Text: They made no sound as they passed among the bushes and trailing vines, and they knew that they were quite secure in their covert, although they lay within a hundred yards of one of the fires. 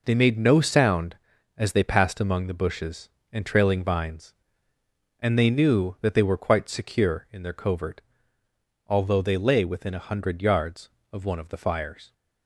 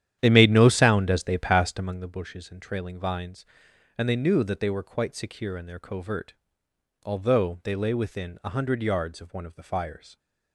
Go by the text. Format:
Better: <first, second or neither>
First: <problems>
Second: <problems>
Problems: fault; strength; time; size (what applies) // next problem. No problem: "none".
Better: first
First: none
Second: starts louder than the rest; strong; until 2.0 s; 10.5 dB